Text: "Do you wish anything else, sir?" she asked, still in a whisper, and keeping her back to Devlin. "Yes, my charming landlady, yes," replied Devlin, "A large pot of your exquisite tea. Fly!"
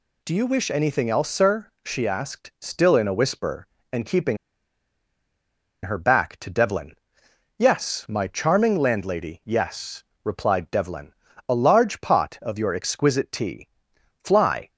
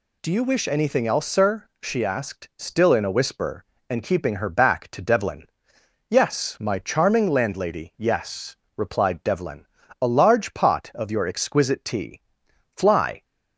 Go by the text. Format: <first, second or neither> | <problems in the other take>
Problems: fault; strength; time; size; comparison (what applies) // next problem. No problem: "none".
second | pauses between "keeping" and "her"; strong; at 4.3 s; 1.4 s long